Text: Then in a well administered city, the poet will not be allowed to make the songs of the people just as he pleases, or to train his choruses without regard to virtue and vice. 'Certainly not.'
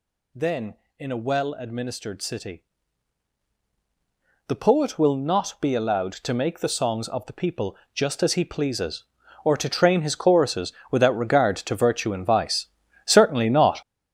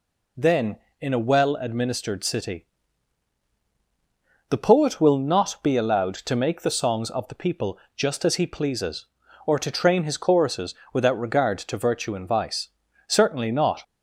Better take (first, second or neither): second